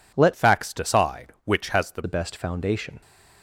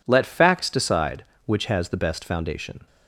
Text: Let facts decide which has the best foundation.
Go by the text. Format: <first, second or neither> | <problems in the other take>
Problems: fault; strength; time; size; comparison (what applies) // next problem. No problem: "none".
second | changes voice from "facts" to "the"; from 0.3 to 2.0 s; 1.7 s long